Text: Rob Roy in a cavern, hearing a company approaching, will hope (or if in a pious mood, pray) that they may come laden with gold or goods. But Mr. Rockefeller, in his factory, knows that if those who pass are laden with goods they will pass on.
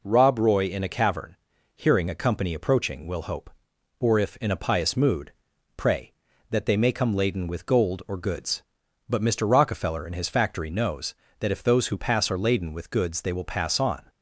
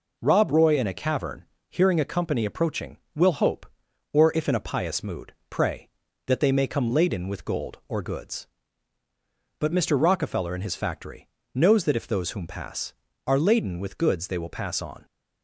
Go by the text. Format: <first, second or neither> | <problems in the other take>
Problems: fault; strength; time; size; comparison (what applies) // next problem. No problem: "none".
first | says "whom" for "who"; at 12.3 s